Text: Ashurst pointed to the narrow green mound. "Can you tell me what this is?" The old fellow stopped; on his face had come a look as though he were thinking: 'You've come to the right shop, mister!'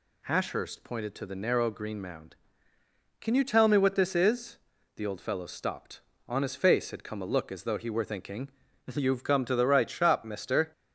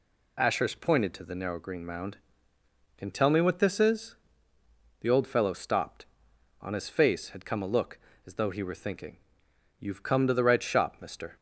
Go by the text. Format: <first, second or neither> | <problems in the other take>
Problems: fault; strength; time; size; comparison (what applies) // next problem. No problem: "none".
first | skips "you"; at 3.1 s